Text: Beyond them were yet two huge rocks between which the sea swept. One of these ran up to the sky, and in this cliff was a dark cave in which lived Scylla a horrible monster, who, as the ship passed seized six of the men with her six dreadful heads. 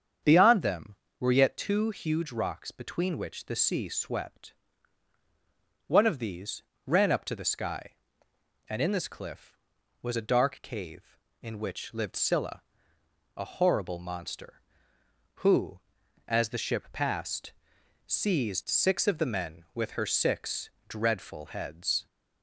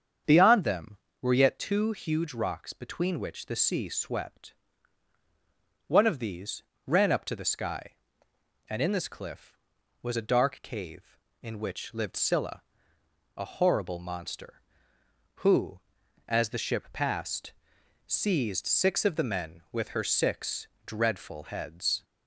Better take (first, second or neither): neither